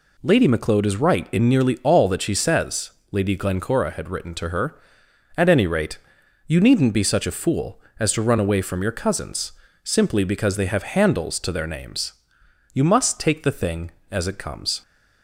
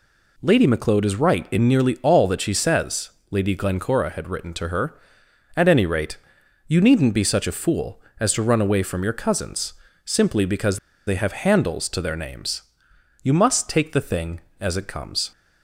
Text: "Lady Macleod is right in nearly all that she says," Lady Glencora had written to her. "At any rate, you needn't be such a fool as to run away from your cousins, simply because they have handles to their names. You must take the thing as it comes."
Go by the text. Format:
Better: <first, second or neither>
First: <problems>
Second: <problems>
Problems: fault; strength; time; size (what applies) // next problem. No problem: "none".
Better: first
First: none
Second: pauses between "because" and "they"; slight; at 10.7 s; 0.29 s long